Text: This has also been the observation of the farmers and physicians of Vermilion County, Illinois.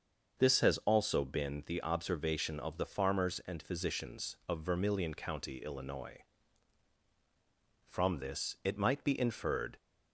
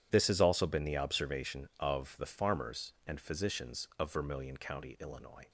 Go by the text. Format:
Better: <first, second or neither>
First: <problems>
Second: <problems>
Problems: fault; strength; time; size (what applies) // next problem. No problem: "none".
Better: second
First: starts louder than the rest; until 1.4 s; 6.5 dB // goes on to say "From this it might be inferred"; strong; from 7.8 s on; 1.9 s long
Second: none